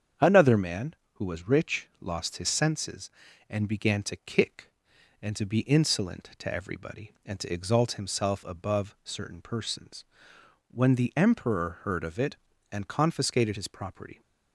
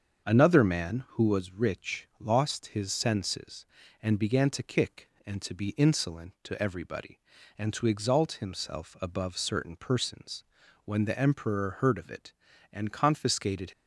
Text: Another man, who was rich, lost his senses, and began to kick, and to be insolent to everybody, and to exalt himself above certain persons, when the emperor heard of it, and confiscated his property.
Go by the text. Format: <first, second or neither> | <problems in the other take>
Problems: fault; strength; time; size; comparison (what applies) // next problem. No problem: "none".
first | starts louder than the rest; until 1.3 s; 7 dB; strong in the first // stops before "his property"; at 13.7 s